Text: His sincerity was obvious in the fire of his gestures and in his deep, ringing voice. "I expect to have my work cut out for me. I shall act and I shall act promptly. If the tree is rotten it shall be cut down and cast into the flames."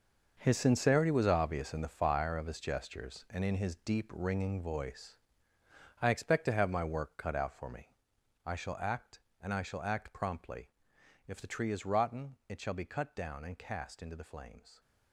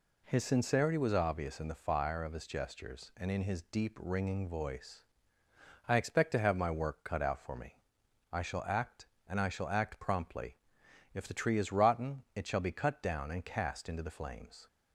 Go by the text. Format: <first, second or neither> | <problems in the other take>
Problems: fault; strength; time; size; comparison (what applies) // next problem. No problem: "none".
second | gets quieter; strong; throughout; 12.5 dB